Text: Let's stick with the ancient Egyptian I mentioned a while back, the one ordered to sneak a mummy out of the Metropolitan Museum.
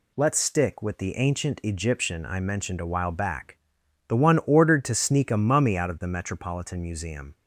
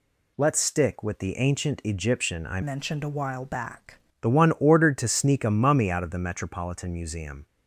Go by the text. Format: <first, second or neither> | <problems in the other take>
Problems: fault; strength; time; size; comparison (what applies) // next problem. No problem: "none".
first | changes voice from "mentioned" to "back"; from 2.6 to 3.9 s; 1.3 s long